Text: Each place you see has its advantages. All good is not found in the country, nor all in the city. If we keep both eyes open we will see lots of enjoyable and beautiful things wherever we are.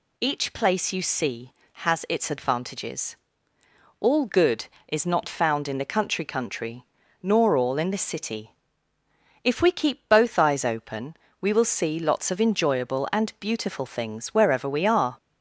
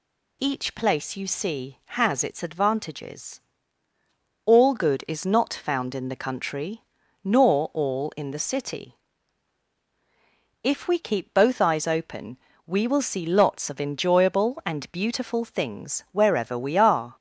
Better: second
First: says "country" twice; at 6.2 s // pauses between "open" and "we"; slight; at 11.1 s; 0.24 s long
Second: pauses between "open" and "we"; slight; at 12.3 s; 0.28 s long

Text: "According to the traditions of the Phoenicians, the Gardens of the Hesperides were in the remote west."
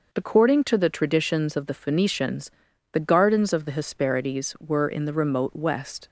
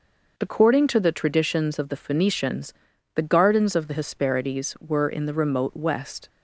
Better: neither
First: none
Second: none

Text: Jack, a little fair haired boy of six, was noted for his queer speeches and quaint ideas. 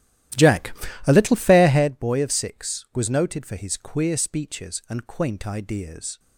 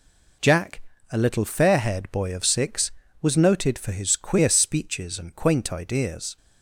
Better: second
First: starts louder than the rest; strong; until 1.9 s; 13.5 dB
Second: none

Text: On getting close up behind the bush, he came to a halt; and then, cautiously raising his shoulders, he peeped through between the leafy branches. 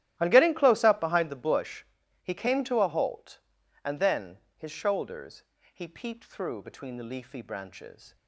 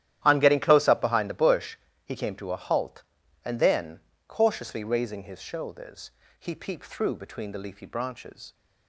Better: second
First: starts louder than the rest; strong; until 1.2 s; 13.5 dB // skips "cautiously raising"; at 4.4 s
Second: starts louder than the rest; strong; until 1.2 s; 12 dB

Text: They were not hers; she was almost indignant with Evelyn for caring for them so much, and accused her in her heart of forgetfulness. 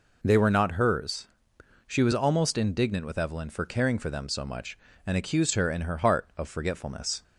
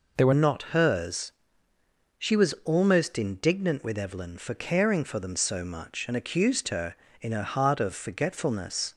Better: first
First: none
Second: changes voice at "not"; from 0.3 s on; 8.6 s long

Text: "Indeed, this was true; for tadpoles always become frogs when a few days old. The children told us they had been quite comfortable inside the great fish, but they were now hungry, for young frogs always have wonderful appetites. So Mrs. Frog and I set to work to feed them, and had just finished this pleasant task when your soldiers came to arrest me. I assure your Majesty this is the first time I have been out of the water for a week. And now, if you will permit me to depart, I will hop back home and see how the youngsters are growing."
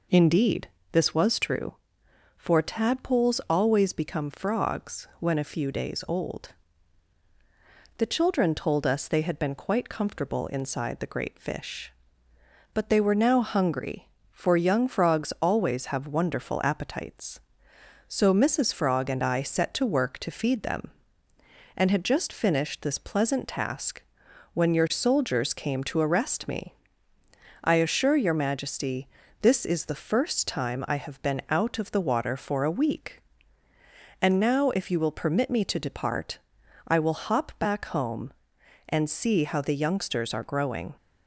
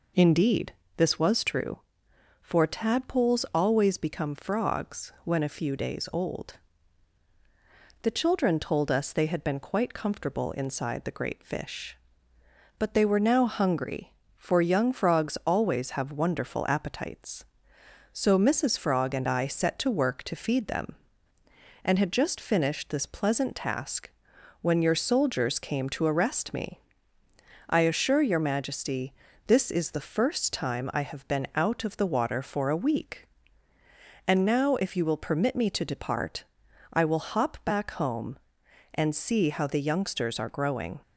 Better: neither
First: pauses between "task" and "when"; noticeable; at 24.0 s; 0.52 s long // pauses between "Majesty" and "this"; slight; at 29.0 s; 0.36 s long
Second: pauses between "task" and "when"; noticeable; at 24.1 s; 0.52 s long // pauses between "Majesty" and "this"; slight; at 29.1 s; 0.36 s long

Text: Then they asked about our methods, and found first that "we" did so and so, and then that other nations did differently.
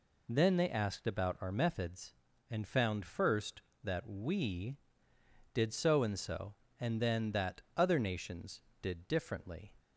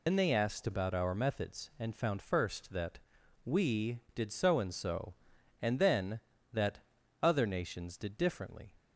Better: first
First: pauses between "that" and "other"; slight; at 7.6 s; 0.16 s long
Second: loses the start of "Then"; at 0.0 s; 75 ms // pauses between "that" and "we"; noticeable; at 2.9 s; 0.46 s long // pauses between "that" and "other"; at 6.8 s; 0.42 s long

